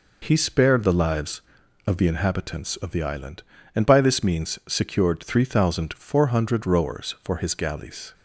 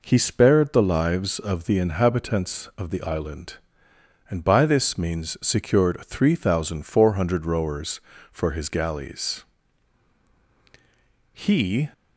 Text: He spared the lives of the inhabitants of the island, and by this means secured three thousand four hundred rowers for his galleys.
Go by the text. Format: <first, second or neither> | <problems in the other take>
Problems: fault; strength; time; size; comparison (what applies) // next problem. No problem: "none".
first | goes on to say "He"; from 11.3 s on; 0.60 s long